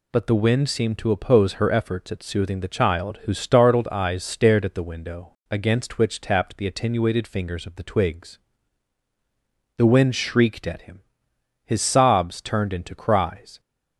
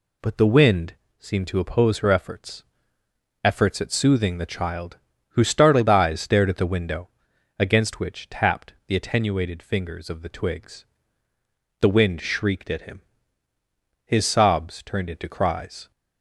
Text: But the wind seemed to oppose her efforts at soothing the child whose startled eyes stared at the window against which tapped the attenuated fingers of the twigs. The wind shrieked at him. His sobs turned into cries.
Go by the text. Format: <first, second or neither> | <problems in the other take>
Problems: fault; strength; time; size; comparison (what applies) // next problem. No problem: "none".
first | pauses between "wind" and "seemed"; slight; at 0.9 s; 0.26 s long // says "efforts" twice; at 3.4 s // pauses between "child" and "whose"; slight; at 4.9 s; 0.32 s long // pauses between "window" and "against"; noticeable; at 7.0 s; 0.48 s long; slight in the first